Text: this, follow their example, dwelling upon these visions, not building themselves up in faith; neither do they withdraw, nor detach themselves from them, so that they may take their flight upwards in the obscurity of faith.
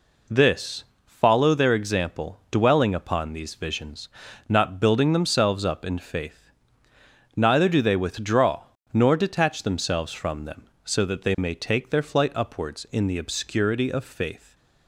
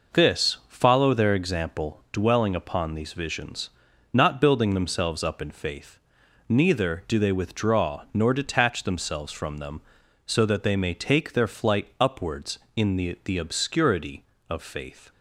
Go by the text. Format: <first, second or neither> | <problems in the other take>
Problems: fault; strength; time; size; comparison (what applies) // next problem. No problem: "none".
first | says "the" twice; at 13.2 s